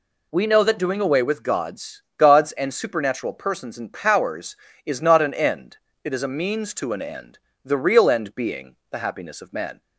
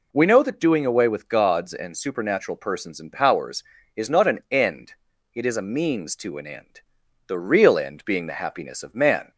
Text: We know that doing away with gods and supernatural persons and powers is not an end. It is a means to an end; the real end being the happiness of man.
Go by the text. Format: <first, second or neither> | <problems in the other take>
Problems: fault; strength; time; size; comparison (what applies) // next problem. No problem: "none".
second | says "gods" twice; at 2.1 s // pauses between "being" and "the"; slight; at 8.7 s; 0.16 s long